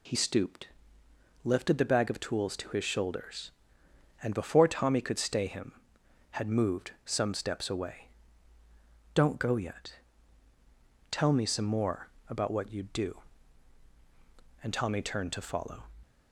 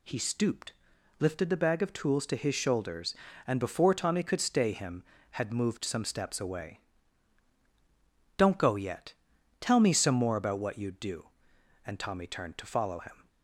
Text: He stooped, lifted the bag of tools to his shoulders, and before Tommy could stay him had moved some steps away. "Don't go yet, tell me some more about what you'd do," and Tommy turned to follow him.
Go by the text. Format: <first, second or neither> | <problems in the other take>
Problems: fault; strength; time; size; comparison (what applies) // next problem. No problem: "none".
second | pauses between "moved" and "some"; slight; at 6.9 s; 0.16 s long // pauses between "more" and "about"; slight; at 12.1 s; 0.18 s long // stops before "him"; at 16.0 s